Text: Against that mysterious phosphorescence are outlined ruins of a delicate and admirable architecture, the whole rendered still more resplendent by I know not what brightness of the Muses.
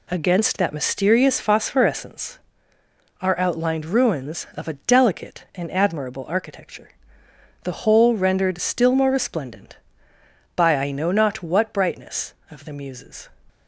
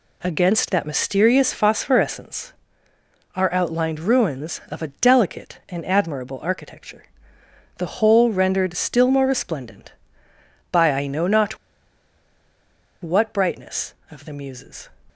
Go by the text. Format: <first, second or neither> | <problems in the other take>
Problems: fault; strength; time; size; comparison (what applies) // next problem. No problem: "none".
first | pauses between "not" and "what"; strong; at 11.5 s; 1.4 s long